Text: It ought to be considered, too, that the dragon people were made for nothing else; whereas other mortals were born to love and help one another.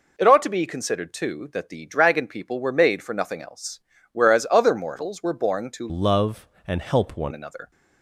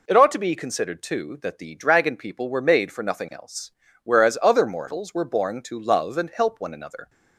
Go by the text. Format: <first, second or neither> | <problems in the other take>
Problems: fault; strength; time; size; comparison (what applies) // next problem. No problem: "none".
second | changes voice from "love" to "one"; from 5.8 to 7.3 s; 1.5 s long